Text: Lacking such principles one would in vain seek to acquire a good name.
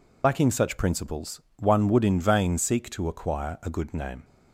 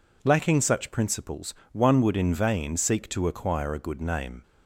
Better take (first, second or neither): second